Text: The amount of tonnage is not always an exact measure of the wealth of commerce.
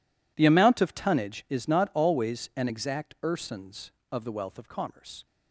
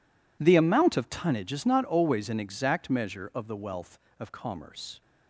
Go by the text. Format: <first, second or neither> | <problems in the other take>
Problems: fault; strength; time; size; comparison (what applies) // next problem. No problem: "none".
second | says "ersons" for "measure"; at 3.2 s